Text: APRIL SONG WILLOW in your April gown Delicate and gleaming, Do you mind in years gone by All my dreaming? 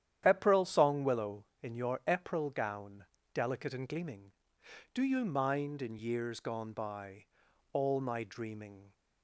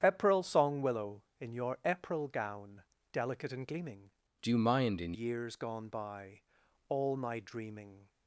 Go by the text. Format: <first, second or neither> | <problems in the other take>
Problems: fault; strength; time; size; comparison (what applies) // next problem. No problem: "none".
first | starts louder than the rest; strong; until 1.0 s; 8.5 dB; strong in the first // pauses between "gown" and "Delicate"; slight; at 2.8 s; 0.30 s long; slight in the first // changes voice from "Do" to "in"; from 4.4 to 5.1 s; 0.7 s long // pauses between "by" and "All"; noticeable; at 6.4 s; 0.48 s long; noticeable in the first